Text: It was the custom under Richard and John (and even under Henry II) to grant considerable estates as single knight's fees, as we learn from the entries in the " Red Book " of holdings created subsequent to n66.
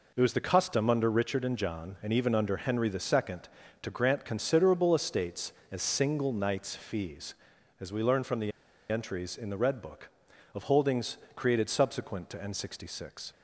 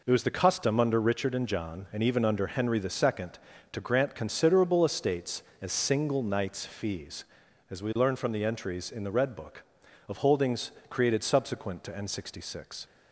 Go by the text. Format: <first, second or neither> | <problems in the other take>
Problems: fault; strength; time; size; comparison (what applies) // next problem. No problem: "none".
second | pauses between "the" and "entries"; at 8.5 s; 0.40 s long // pauses between "holdings" and "created"; slight; at 11.1 s; 0.20 s long; slight in the second